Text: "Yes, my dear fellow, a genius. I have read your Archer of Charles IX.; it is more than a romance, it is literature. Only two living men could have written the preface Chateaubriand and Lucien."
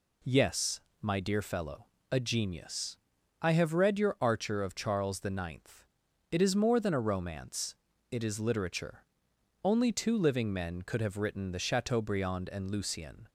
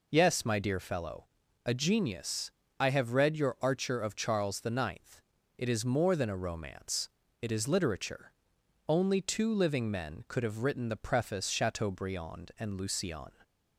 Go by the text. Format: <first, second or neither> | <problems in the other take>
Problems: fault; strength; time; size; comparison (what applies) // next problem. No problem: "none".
second | skips "preface"; at 11.5 s